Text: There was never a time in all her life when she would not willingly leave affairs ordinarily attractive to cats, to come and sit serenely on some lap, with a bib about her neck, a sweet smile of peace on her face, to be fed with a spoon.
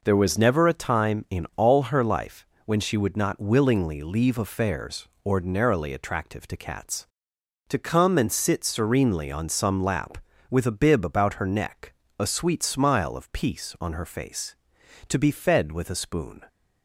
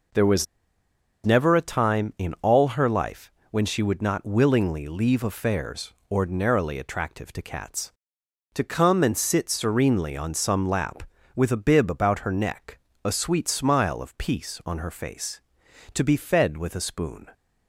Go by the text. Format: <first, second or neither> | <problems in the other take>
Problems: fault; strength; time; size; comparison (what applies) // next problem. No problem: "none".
first | pauses between "was" and "never"; noticeable; at 0.4 s; 0.81 s long // pauses between "life" and "when"; slight; at 3.3 s; 0.20 s long; slight in the first // pauses between "affairs" and "ordinarily"; slight; at 5.9 s; 0.18 s long; slight in the first